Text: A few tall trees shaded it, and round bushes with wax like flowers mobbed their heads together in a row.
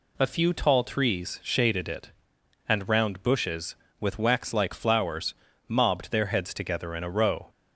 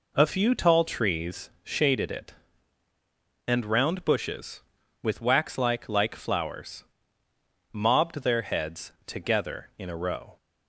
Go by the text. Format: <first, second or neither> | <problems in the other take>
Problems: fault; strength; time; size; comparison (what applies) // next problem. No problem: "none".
first | says "like" twice; at 5.8 s // pauses between "flowers" and "mobbed"; noticeable; at 6.8 s; 0.88 s long; slight in the first